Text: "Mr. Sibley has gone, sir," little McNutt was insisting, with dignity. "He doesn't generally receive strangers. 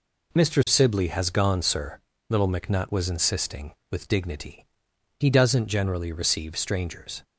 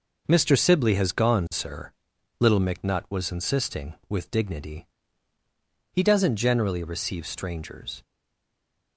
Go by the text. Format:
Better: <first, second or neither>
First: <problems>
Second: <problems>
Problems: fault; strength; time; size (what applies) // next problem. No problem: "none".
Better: first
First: none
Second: stays silent after the last word; slight; from 8.0 s on; 0.9 s long